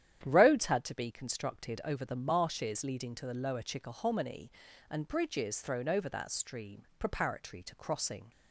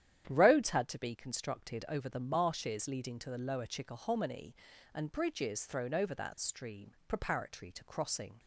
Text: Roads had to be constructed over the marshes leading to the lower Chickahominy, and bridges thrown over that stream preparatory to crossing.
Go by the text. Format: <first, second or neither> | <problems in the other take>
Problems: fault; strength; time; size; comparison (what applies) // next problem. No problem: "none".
neither | starts louder than the rest; strong; the same in both // pauses between "stream" and "preparatory"; slight; the same in both